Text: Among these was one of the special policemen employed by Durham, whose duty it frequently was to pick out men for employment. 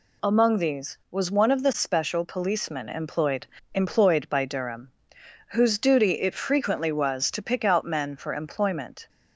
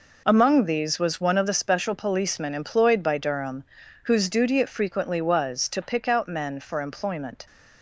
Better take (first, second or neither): second